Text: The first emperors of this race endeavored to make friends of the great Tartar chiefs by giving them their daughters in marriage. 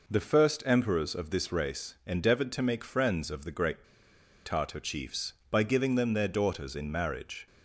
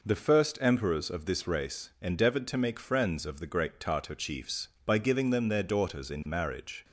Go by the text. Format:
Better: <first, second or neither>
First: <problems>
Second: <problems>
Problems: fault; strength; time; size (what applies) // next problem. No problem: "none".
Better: second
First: pauses between "great" and "Tartar"; noticeable; at 3.8 s; 0.61 s long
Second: none